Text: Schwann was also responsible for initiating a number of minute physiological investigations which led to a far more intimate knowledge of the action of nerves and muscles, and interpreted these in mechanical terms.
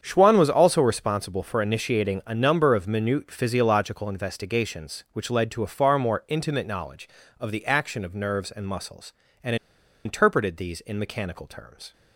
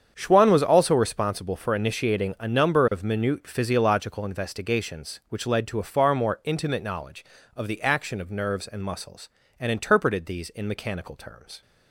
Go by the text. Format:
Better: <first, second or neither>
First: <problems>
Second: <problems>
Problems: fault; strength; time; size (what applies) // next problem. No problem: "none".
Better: second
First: starts louder than the rest; strong; until 1.0 s; 7.5 dB // pauses between "and" and "interpreted"; noticeable; at 9.5 s; 0.50 s long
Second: starts louder than the rest; strong; until 1.1 s; 7.5 dB